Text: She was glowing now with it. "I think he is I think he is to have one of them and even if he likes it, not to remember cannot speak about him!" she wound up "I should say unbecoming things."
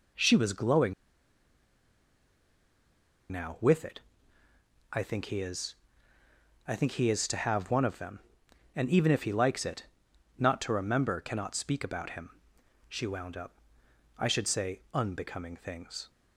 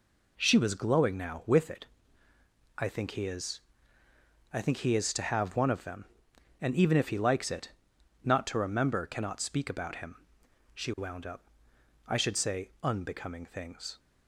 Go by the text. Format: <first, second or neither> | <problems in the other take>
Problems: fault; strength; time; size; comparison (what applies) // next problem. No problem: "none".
second | pauses between "glowing" and "now"; strong; at 0.9 s; 2.3 s long // pauses between "is" and "I"; noticeable; at 5.7 s; 0.90 s long; noticeable in the second // pauses between "up" and "I"; noticeable; at 13.5 s; 0.64 s long; noticeable in the second